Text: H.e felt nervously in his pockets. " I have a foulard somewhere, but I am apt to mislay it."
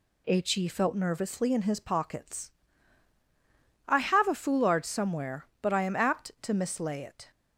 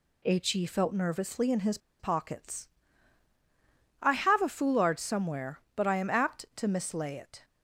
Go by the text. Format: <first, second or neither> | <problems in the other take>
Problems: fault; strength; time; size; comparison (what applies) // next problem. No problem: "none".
first | pauses between "his" and "pockets"; slight; at 1.7 s; 0.22 s long